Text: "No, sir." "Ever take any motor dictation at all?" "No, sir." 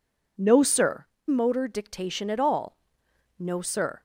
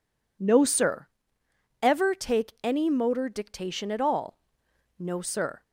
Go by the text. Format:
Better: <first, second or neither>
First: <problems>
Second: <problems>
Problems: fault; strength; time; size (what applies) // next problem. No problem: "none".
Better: second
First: skips "Ever take any"; at 1.1 s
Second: none